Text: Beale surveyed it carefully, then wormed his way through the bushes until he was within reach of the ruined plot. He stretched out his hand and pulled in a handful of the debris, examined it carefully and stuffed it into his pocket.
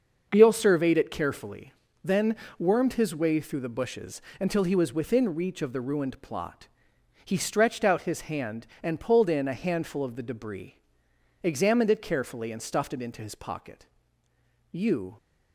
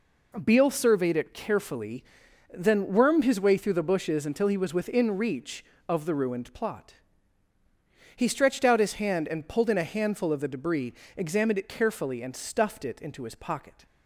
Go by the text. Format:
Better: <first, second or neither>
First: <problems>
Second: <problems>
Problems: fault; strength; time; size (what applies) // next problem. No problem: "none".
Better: second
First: starts louder than the rest; until 1.3 s; 6.5 dB // pauses between "then" and "wormed"; slight; at 2.3 s; 0.24 s long // pauses between "bushes" and "until"; slight; at 4.2 s; 0.18 s long // goes on to say "You"; slight; from 14.7 s on; 0.46 s long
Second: none